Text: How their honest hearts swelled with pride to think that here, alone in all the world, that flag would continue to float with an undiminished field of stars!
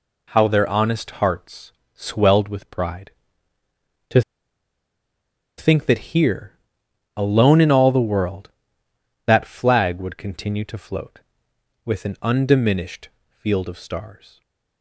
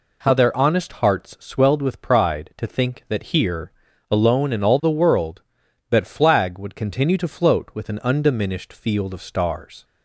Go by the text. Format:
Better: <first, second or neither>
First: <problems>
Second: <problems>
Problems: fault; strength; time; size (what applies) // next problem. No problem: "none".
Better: second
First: pauses between "honest" and "hearts"; slight; at 1.0 s; 0.16 s long // pauses between "hearts" and "swelled"; slight; at 1.7 s; 0.22 s long // pauses between "to" and "think"; strong; at 4.2 s; 1.3 s long // pauses between "undiminished" and "field"; slight; at 13.0 s; 0.22 s long // stays silent after the last word; slight; from 14.3 s on; 0.5 s long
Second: none